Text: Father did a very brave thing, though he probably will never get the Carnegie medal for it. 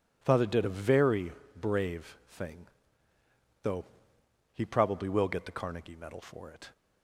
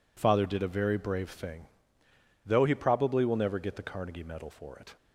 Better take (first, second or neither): second